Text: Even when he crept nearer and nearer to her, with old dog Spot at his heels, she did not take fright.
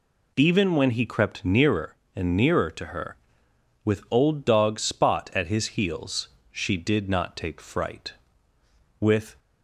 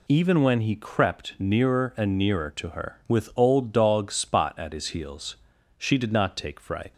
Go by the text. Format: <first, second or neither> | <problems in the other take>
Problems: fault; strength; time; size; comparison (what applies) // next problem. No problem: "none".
second | goes on to say "With"; slight; from 8.9 s on; 0.36 s long